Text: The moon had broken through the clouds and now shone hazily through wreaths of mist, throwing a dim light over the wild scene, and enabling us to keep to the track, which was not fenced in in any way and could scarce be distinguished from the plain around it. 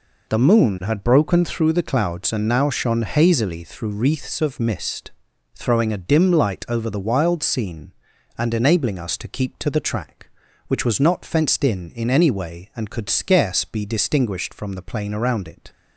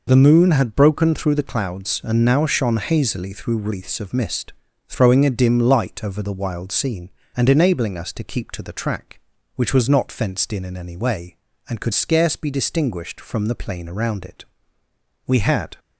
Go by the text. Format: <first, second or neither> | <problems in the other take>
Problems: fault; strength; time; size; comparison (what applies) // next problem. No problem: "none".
first | goes on to say "We had"; slight; from 15.2 s on; 0.48 s long